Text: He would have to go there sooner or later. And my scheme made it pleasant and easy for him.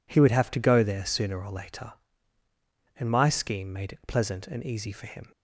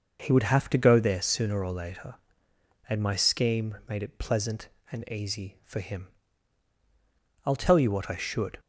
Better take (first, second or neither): first